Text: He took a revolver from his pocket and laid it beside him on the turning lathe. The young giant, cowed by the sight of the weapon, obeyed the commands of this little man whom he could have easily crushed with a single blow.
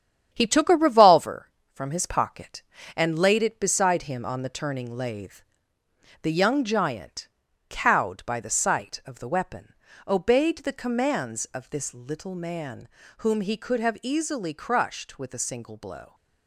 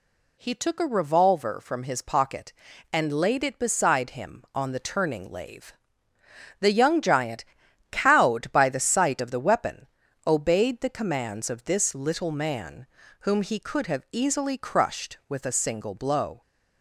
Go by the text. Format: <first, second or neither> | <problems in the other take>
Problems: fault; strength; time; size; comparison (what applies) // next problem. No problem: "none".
second | gets quieter; throughout; 7 dB // pauses between "man" and "whom"; slight; at 12.8 s; 0.32 s long; slight in the second